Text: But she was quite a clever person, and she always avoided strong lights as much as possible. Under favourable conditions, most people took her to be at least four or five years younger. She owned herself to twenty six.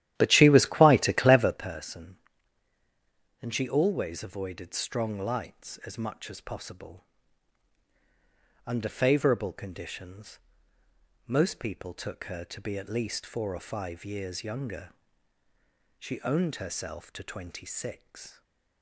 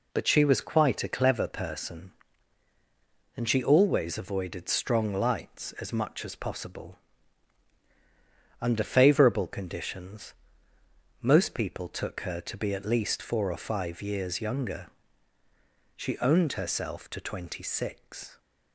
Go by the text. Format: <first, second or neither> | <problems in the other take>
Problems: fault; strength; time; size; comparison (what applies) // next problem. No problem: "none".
second | starts louder than the rest; strong; until 1.7 s; 12.5 dB // stays silent after the last word; slight; from 18.3 s on; 0.5 s long